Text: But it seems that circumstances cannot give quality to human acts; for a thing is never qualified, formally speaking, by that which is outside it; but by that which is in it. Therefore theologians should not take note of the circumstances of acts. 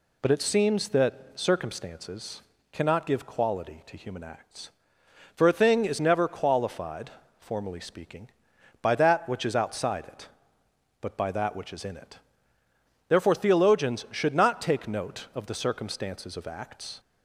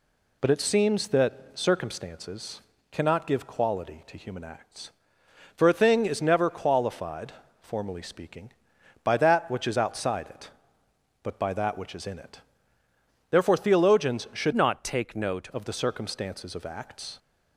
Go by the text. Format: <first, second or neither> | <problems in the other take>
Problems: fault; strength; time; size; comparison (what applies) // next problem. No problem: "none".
first | pauses between "circumstances" and "cannot"; slight; at 2.6 s; 0.30 s long; slight in the first // changes voice from "not" to "note"; from 14.5 to 15.4 s; 0.9 s long